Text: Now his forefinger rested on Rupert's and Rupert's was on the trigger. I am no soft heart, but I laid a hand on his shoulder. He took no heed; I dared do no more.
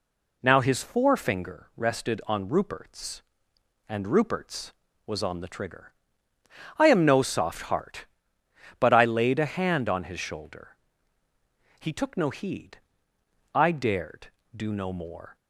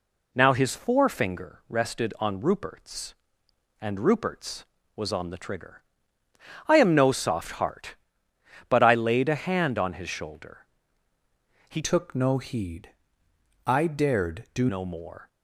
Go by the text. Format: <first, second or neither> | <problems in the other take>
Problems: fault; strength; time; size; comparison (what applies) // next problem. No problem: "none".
first | changes voice from "took" to "do"; from 11.8 to 14.6 s; 2.8 s long